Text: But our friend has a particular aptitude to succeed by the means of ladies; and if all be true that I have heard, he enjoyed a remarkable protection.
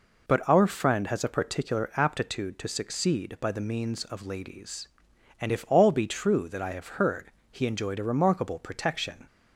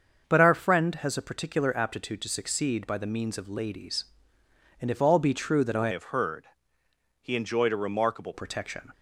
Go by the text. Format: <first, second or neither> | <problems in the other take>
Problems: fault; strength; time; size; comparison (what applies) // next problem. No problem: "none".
first | starts louder than the rest; until 1.2 s; 6.5 dB // changes voice from "have" to "remarkable"; from 5.9 to 8.3 s; 2.4 s long